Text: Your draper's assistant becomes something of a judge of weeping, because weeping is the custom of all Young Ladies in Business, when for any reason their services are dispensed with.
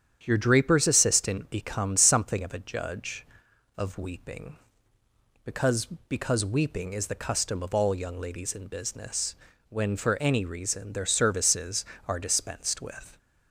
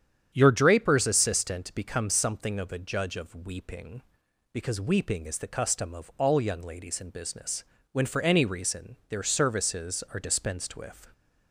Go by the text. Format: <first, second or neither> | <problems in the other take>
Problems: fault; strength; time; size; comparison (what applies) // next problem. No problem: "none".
second | starts louder than the rest; strong; until 1.2 s; 8.5 dB; strong in the second // says "because" twice; at 6.0 s